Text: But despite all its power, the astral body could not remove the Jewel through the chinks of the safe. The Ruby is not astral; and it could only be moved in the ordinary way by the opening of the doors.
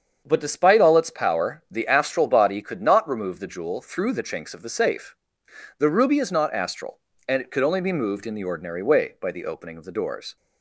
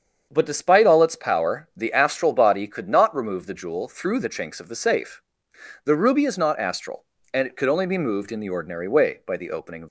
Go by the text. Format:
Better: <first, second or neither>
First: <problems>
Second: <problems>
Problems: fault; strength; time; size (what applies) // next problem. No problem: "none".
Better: first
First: starts louder than the rest; strong; until 1.2 s; 7.5 dB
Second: starts louder than the rest; strong; until 1.3 s; 7 dB // stops before "the doors"; at 9.8 s